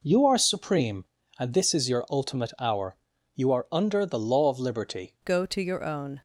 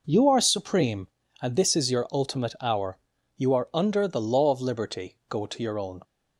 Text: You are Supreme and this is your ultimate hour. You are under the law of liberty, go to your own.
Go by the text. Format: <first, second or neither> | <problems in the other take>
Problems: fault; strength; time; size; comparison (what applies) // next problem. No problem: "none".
second | changes voice at "go"; from 5.2 s on; 1.0 s long